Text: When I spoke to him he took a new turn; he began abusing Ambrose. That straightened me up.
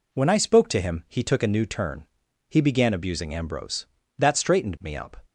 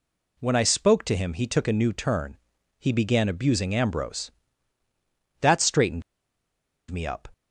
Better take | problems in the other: first | pauses between "straightened" and "me"; noticeable; at 6.0 s; 0.88 s long

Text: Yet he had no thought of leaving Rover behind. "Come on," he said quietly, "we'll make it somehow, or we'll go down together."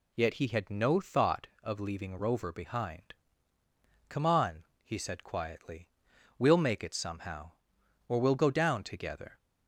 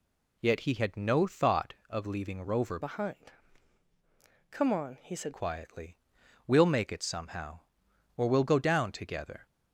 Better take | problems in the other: first | changes voice from "behind" to "said"; from 2.7 to 5.3 s; 2.6 s long

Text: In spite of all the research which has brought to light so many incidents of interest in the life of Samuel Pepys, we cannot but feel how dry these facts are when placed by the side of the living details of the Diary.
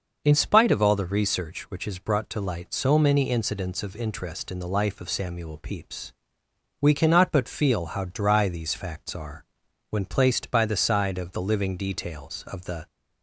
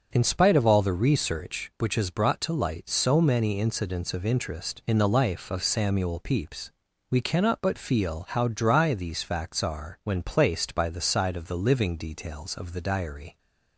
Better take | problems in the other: second | starts louder than the rest; noticeable; until 1.2 s; 6 dB; also in the second // pauses between "are" and "when"; noticeable; at 9.4 s; 0.46 s long // stops before "Diary"; at 12.8 s

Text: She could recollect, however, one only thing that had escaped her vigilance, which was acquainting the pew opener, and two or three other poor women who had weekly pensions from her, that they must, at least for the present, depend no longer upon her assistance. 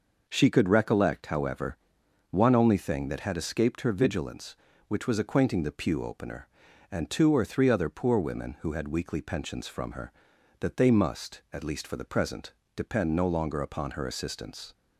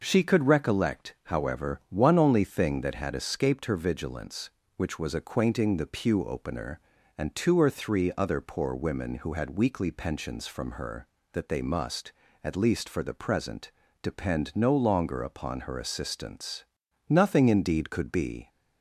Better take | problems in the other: first | goes on to say "Nothing indeed could be"; from 17.0 s on; 1.4 s long

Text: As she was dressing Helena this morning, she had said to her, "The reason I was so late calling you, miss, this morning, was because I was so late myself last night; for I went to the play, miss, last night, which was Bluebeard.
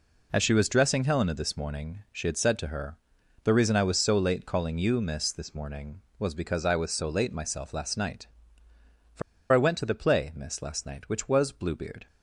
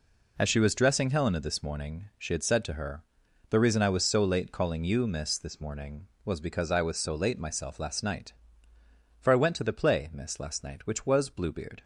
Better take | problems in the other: second | pauses between "for" and "I"; slight; at 9.2 s; 0.30 s long

